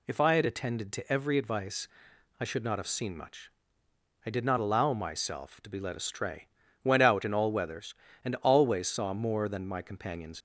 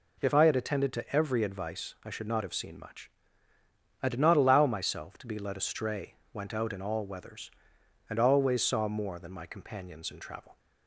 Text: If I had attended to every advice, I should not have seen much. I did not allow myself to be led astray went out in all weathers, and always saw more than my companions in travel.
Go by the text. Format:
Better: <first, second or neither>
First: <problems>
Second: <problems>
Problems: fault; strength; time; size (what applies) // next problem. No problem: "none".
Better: second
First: pauses between "astray" and "went"; slight; at 6.4 s; 0.36 s long // stops before "in travel"; at 10.3 s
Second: pauses between "astray" and "went"; slight; at 6.1 s; 0.20 s long